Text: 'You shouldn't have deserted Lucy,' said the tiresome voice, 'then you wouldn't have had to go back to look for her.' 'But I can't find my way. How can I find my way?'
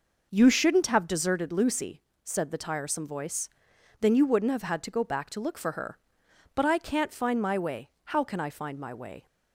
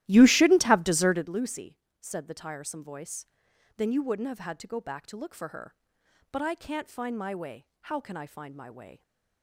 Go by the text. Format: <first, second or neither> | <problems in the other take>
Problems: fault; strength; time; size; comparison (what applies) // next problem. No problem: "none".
first | starts louder than the rest; strong; until 1.3 s; 14.5 dB